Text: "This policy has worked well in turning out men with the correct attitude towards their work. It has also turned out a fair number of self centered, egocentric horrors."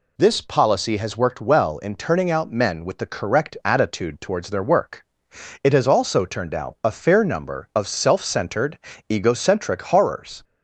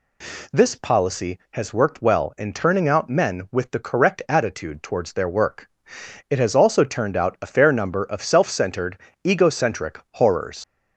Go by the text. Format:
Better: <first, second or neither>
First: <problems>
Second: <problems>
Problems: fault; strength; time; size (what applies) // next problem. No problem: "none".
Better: first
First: none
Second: leaves "horrors" unfinished; at 10.6 s; 95 ms